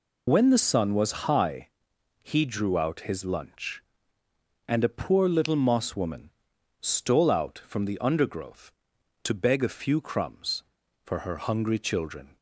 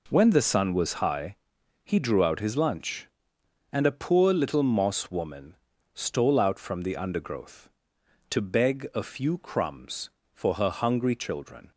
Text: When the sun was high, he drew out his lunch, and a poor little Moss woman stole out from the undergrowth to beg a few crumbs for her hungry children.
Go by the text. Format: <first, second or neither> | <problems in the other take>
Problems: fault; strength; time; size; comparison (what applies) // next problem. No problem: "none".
second | loses the start of "When"; at 0.2 s; 45 ms // pauses between "woman" and "stole"; noticeable; at 6.2 s; 0.50 s long; also in the second